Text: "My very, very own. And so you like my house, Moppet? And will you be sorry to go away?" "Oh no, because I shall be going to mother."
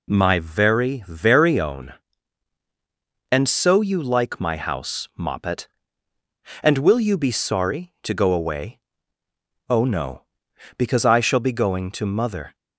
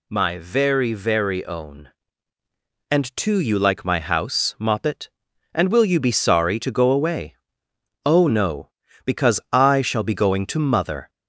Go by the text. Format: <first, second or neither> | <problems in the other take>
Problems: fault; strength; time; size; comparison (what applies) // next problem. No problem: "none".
first | says "too" for "so"; at 3.1 s